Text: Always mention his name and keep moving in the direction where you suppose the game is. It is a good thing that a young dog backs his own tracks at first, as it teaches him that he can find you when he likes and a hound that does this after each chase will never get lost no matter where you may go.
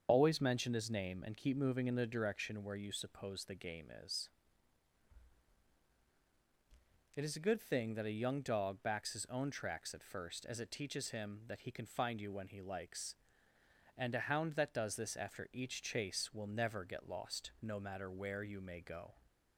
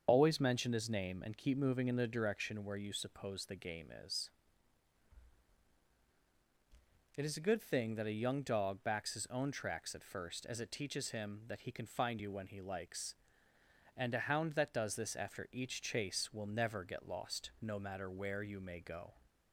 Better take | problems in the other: neither | starts louder than the rest; the same in both

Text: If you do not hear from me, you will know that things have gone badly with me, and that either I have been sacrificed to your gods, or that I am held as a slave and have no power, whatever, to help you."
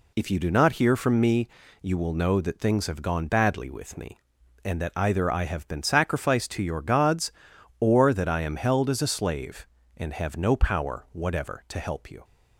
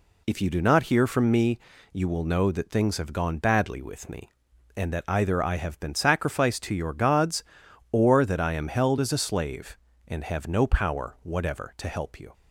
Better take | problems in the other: neither | none

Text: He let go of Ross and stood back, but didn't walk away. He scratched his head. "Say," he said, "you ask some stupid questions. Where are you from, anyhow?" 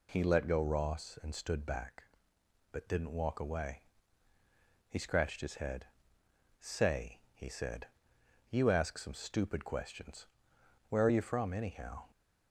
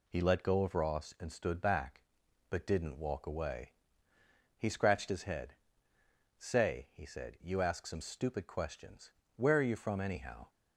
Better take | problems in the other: second | skips "of"; at 0.5 s

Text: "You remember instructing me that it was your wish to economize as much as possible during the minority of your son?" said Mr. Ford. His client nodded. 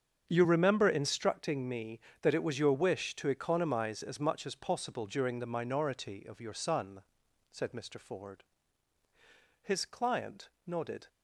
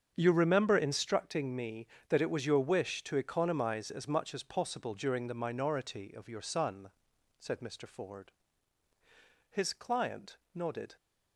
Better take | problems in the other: neither | starts louder than the rest; strong; the same in both // pauses between "client" and "nodded"; slight; the same in both

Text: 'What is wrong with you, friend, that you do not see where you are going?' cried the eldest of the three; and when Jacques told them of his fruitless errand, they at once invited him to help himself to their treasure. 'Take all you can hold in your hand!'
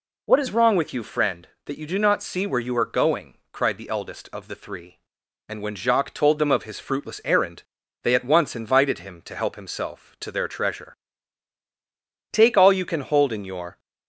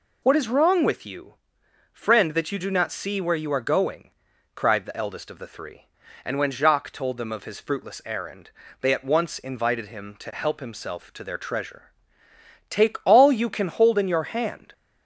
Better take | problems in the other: second | stops before "hand"; at 13.7 s

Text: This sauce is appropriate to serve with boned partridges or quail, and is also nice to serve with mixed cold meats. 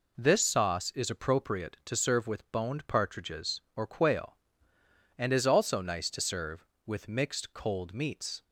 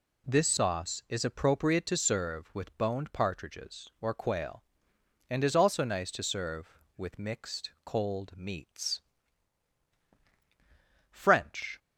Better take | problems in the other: first | goes on to say "FRENCH"; noticeable; from 11.1 s on; 0.68 s long

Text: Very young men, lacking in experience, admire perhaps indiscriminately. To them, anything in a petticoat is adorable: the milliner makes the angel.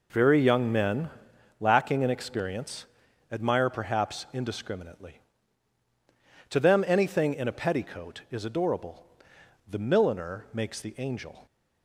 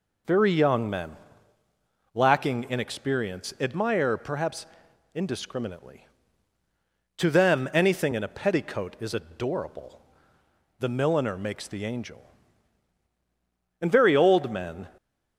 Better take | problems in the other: first | pauses between "perhaps" and "indiscriminately"; noticeable; at 4.6 s; 0.48 s long // goes on to say "And very old men"; noticeable; from 13.8 s on; 1.0 s long

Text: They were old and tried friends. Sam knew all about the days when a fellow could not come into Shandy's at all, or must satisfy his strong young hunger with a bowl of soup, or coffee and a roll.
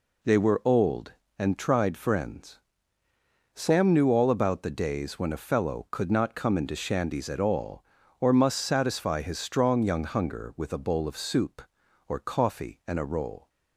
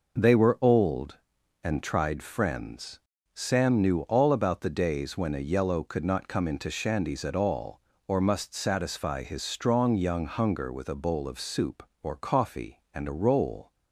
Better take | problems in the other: first | says "yellow" for "fellow"; at 5.4 s

